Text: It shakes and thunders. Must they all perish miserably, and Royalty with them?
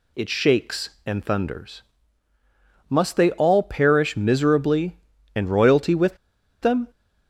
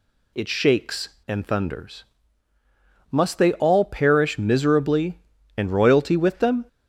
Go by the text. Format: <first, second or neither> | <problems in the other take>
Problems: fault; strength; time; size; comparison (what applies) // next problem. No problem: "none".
second | pauses between "with" and "them"; at 6.1 s; 0.44 s long